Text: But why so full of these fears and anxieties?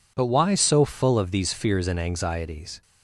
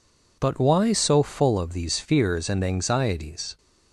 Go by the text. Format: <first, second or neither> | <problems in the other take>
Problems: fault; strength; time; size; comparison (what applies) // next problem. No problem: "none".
neither | none